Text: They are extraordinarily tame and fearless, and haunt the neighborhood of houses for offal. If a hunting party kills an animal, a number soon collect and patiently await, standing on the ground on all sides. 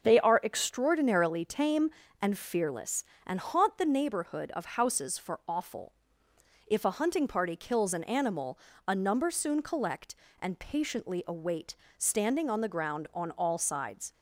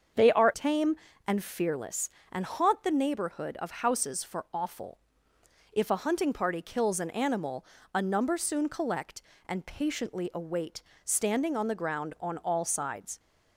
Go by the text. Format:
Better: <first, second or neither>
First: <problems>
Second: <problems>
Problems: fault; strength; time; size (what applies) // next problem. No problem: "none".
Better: first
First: starts louder than the rest; until 1.0 s; 6.5 dB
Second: starts louder than the rest; until 1.4 s; 6.5 dB // skips "extraordinarily"; at 0.5 s